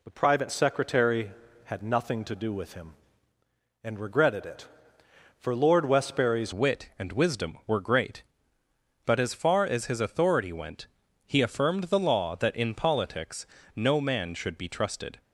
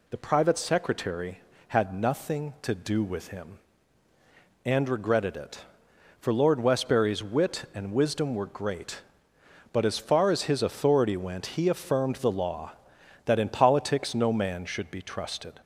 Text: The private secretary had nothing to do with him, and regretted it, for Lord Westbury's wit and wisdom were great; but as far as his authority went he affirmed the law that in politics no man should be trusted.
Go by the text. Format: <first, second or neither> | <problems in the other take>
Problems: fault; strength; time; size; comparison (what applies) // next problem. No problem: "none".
second | changes voice at "wit"; from 6.5 s on; 8.7 s long // pauses between "went" and "he"; at 10.8 s; 0.38 s long // pauses between "politics" and "no"; slight; at 13.4 s; 0.28 s long